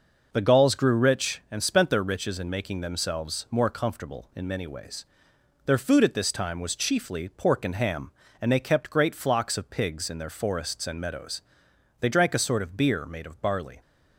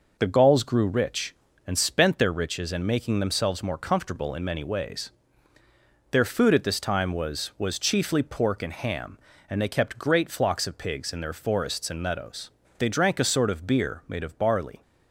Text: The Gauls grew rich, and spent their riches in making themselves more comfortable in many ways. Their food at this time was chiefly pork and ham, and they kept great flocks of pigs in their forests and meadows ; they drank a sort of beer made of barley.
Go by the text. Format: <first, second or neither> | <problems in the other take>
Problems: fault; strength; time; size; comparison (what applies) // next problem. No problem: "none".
first | says "was" twice; at 7.5 s